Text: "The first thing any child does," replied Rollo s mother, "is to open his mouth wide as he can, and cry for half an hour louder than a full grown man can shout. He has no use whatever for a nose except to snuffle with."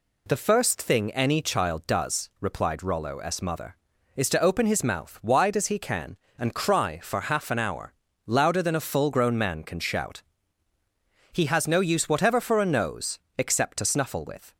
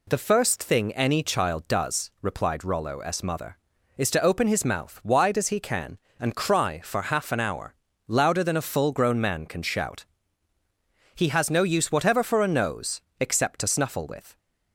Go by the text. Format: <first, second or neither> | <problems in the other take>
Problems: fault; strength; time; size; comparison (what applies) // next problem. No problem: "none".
neither | pauses between "hour" and "louder"; slight; the same in both // pauses between "nose" and "except"; slight; the same in both